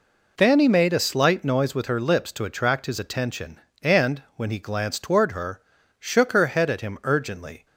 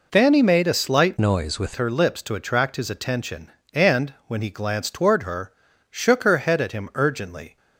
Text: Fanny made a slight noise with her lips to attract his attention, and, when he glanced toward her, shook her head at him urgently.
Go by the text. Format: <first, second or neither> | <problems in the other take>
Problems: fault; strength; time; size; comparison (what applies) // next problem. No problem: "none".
first | changes voice from "noise" to "with"; from 1.1 to 1.7 s; 0.6 s long